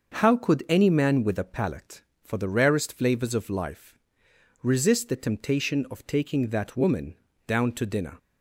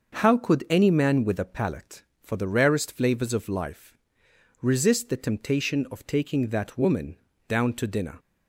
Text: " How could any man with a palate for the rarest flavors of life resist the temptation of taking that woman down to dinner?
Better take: neither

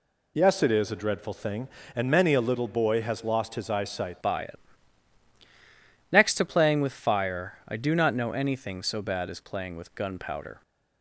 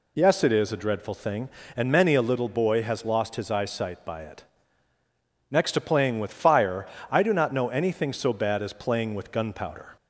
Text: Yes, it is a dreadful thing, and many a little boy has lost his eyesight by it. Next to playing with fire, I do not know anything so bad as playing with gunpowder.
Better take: second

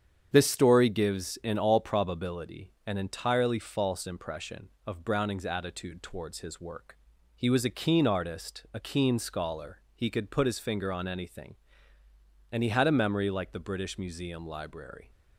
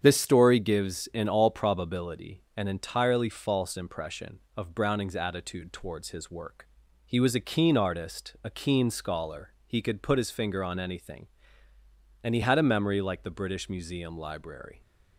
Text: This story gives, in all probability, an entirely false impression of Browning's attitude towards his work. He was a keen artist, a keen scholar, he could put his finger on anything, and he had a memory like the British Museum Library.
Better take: neither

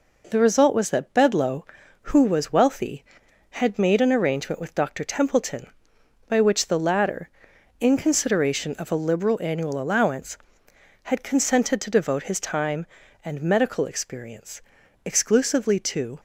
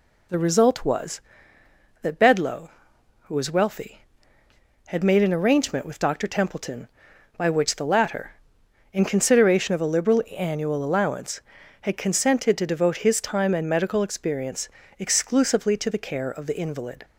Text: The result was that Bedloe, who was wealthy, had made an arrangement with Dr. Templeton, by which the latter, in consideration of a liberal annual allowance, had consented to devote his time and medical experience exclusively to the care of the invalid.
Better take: second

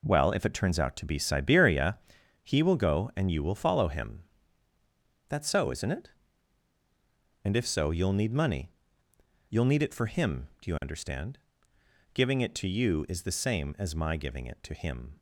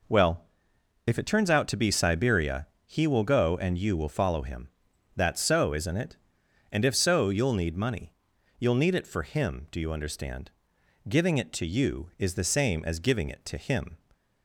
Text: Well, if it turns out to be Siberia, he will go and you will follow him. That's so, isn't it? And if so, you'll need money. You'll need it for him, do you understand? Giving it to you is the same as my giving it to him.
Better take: first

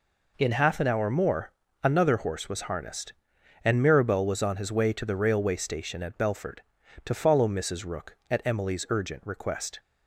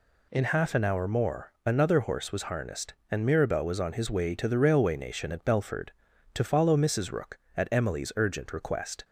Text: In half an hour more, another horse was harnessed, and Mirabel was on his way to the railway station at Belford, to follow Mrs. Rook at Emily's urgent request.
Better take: first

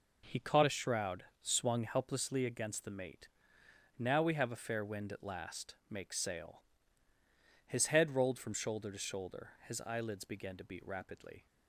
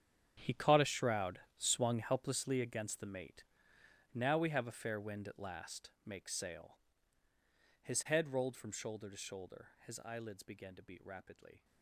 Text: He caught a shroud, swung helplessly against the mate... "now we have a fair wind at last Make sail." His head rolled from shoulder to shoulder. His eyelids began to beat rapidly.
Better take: first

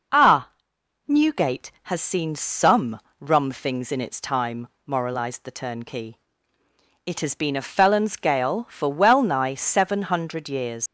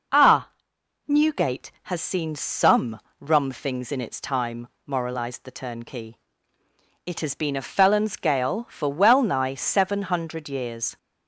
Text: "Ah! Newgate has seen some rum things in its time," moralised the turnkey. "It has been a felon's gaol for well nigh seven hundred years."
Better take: second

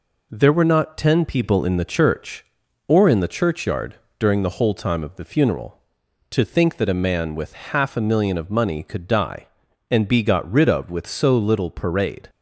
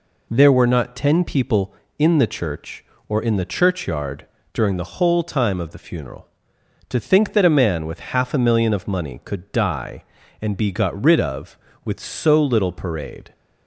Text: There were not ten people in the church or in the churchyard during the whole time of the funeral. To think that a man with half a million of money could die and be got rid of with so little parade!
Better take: neither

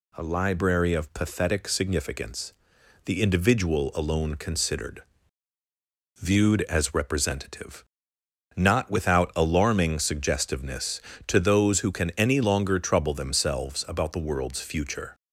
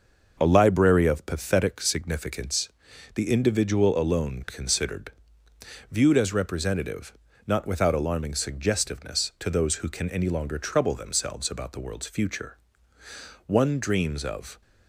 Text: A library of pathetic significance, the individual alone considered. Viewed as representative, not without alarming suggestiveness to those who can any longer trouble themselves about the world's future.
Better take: first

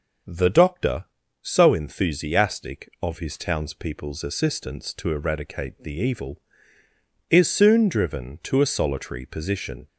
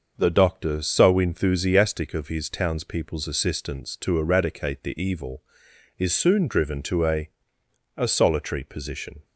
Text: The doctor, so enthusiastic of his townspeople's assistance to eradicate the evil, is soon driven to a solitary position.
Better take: first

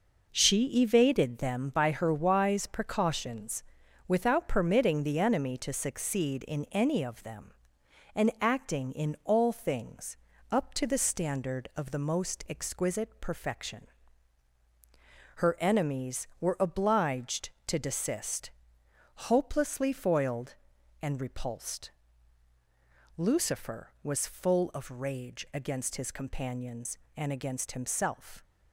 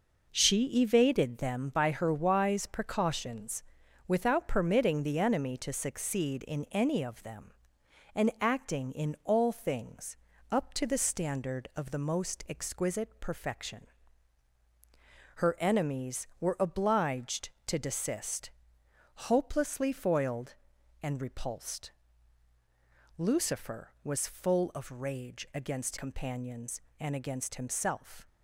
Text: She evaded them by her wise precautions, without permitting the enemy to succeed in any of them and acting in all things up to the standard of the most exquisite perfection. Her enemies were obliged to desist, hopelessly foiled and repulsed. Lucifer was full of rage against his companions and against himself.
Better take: first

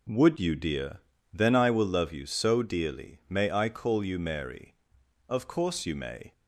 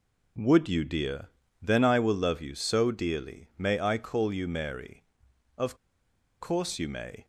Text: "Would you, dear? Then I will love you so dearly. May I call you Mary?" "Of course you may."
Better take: first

